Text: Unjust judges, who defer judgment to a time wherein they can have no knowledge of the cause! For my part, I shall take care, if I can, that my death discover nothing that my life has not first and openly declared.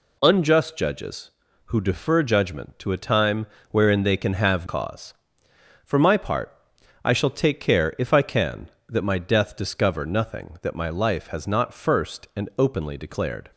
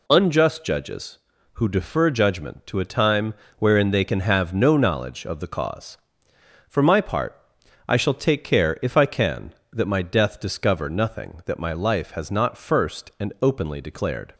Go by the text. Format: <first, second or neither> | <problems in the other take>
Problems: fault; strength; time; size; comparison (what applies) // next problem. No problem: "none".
second | pauses between "time" and "wherein"; slight; at 3.4 s; 0.24 s long; slight in the second // skips "no knowledge of the"; at 4.6 s